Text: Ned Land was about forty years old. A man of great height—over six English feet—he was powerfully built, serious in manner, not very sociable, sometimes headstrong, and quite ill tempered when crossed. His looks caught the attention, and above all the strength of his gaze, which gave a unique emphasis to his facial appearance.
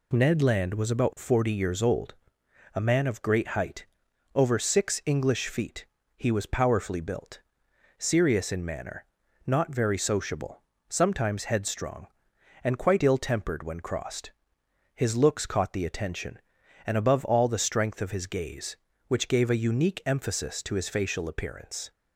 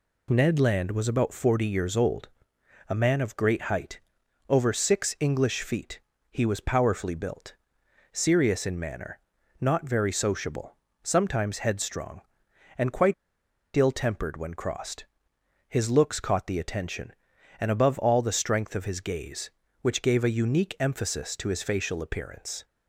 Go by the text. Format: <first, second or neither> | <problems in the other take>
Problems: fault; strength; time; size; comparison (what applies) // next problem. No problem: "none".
first | pauses between "quite" and "ill"; noticeable; at 13.1 s; 0.62 s long